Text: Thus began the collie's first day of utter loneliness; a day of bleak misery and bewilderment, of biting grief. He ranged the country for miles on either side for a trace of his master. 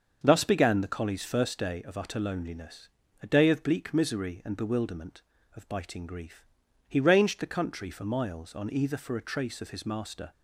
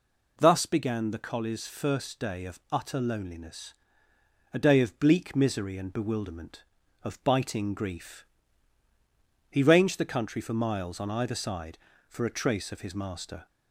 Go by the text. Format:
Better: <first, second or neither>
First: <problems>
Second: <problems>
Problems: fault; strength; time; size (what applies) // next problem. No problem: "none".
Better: second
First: starts louder than the rest; until 1.2 s; 6.5 dB // skips "side"; at 8.9 s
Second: none